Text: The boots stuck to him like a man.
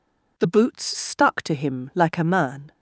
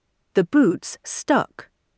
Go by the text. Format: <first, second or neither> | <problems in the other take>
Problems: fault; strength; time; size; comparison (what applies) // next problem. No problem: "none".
first | stops before "to him like a man"; at 1.7 s